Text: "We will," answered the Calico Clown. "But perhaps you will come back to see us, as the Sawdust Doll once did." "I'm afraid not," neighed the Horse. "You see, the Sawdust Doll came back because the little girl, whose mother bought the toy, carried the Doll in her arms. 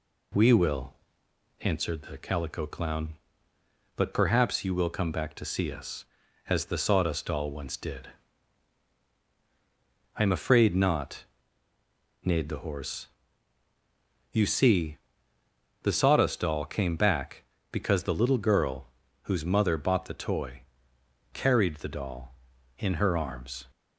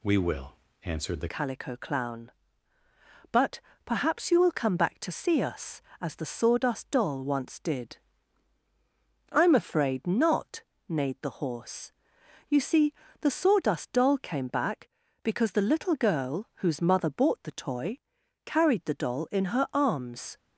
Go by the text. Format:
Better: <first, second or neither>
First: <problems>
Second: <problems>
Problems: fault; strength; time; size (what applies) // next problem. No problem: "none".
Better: first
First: none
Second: changes voice at "Calico"; from 1.2 s on; 19.1 s long // pauses between "But" and "perhaps"; slight; at 3.5 s; 0.26 s long